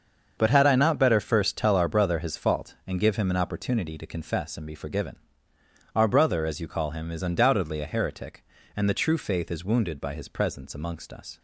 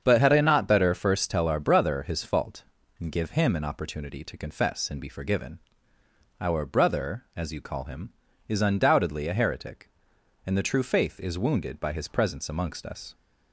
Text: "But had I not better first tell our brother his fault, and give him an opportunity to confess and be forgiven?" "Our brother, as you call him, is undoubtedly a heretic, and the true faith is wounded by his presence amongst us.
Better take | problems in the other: neither | starts louder than the rest; the same in both

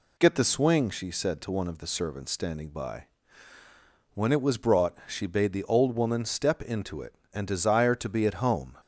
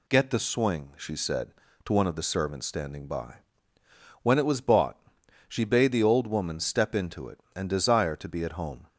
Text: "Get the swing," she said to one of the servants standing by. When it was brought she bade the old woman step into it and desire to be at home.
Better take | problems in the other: first | says "bought" for "brought"; at 4.6 s

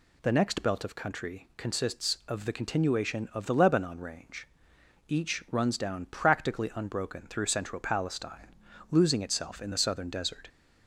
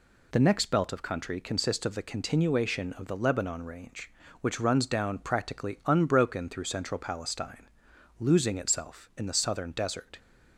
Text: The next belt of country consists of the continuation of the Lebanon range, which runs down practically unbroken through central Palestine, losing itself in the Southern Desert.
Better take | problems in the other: second | says "each" for "which"; at 5.0 s

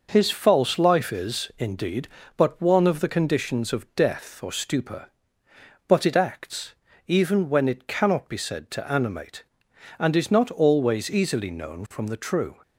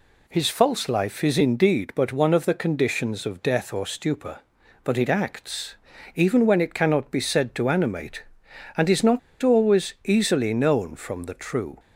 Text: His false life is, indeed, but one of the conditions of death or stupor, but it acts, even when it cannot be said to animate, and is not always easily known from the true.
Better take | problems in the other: first | pauses between "not" and "always"; slight; at 9.1 s; 0.23 s long

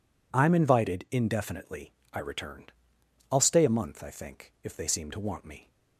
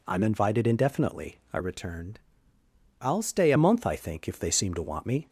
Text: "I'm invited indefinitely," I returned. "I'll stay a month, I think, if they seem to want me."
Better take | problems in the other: first | changes voice from "returned" to "a"; from 1.5 to 3.5 s; 2.0 s long

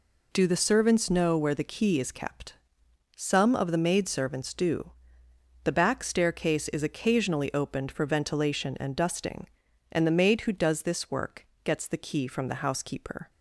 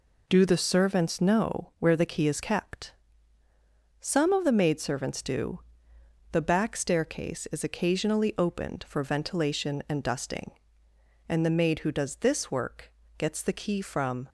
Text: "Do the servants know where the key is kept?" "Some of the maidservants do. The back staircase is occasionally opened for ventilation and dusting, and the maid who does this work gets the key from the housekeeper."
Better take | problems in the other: first | pauses between "work" and "gets"; slight; at 12.9 s; 0.28 s long; slight in the first // stops before "the housekeeper"; at 14.2 s

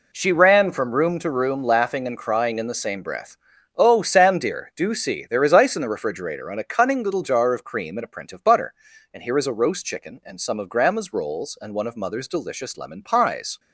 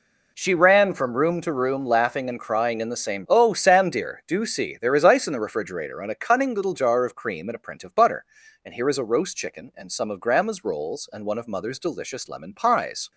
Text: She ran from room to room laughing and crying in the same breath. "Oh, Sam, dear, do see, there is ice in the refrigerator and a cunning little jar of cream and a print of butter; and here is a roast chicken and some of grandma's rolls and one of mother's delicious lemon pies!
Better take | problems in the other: first | skips "breath"; at 3.2 s

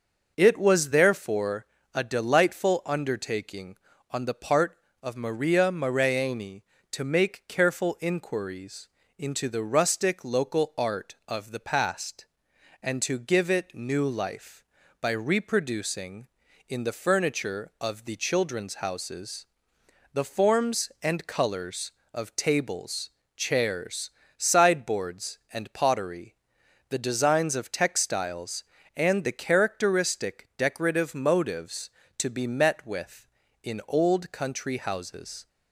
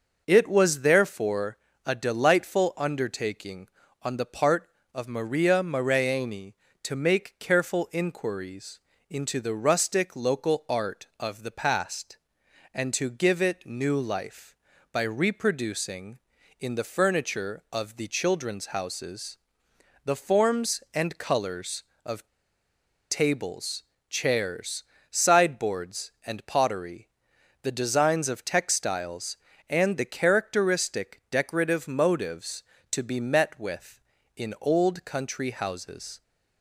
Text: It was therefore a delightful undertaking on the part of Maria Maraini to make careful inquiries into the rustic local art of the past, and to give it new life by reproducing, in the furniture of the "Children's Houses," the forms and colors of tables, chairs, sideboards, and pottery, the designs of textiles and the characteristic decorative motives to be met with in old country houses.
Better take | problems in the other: first | pauses between "therefore" and "a"; slight; at 1.5 s; 0.28 s long; slight in the first // pauses between "inquiries" and "into"; slight; at 8.7 s; 0.30 s long; slight in the first // pauses between "of" and "tables"; noticeable; at 22.2 s; 0.83 s long

